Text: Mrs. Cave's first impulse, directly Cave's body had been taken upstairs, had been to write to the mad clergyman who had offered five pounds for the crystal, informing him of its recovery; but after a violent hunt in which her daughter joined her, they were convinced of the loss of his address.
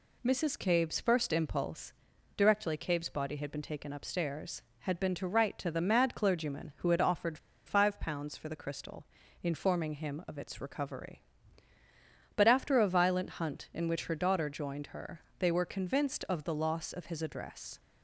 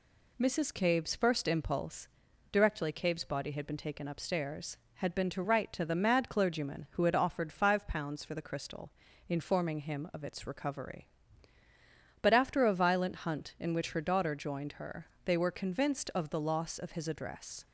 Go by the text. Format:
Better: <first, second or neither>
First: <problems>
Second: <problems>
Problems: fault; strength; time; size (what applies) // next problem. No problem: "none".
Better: second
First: pauses between "offered" and "five"; slight; at 7.3 s; 0.29 s long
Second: none